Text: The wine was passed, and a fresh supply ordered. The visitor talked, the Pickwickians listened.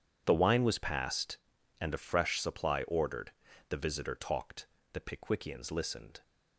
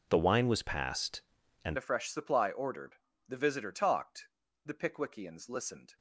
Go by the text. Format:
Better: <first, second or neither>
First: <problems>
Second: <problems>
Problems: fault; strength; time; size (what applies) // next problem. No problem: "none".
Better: first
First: none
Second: changes voice at "a"; from 1.7 s on; 4.2 s long